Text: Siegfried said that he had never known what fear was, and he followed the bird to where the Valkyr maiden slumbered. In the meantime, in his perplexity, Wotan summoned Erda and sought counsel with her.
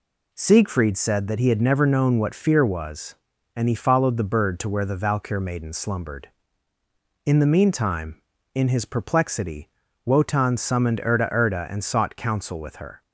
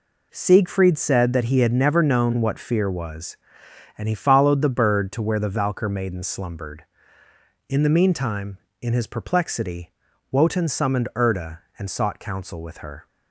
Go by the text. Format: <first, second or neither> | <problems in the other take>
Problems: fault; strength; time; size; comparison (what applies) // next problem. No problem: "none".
second | says "Erda" twice; at 11.2 s